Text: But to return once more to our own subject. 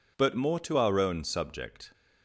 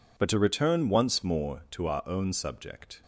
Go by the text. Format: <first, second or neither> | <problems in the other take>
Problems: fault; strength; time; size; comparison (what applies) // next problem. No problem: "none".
second | skips "to return once"; at 0.3 s